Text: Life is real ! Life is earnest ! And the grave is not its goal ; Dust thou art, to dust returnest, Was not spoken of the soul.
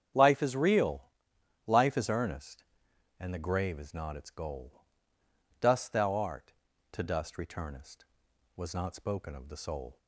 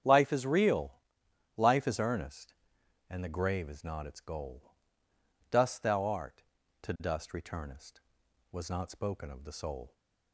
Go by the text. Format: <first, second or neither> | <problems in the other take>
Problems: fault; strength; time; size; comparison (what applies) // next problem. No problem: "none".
neither | starts louder than the rest; strong; the same in both